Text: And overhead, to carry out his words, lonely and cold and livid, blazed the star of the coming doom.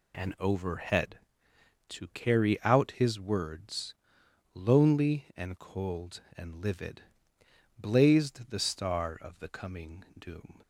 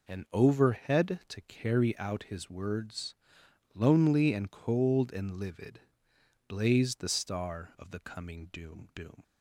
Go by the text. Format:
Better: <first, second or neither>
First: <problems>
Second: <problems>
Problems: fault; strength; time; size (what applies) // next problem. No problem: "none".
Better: first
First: none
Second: says "doom" twice; at 8.9 s